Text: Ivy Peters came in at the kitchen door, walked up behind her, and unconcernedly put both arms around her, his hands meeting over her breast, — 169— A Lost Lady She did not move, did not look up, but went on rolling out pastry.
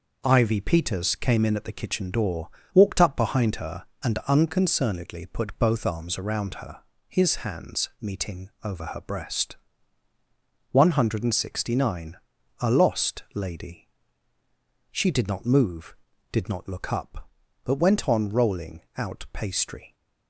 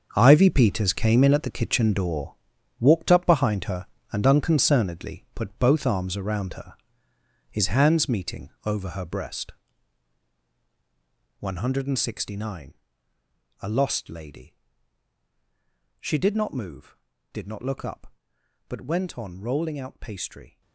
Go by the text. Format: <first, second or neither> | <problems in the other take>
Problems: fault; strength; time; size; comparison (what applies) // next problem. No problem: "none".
first | gets quieter; strong; throughout; 13 dB // pauses between "Lady" and "She"; strong; at 14.5 s; 1.4 s long; also in the first